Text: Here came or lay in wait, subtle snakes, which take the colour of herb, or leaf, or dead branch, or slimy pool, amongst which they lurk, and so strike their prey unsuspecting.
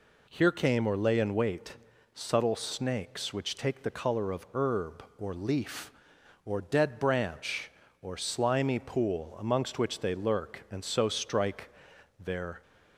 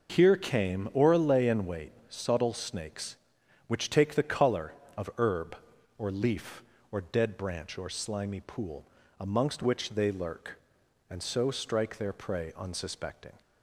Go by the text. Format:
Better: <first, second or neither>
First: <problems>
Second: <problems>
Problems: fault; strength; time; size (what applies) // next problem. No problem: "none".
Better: second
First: pauses between "strike" and "their"; noticeable; at 11.6 s; 0.50 s long // stops before "prey unsuspecting"; at 12.6 s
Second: none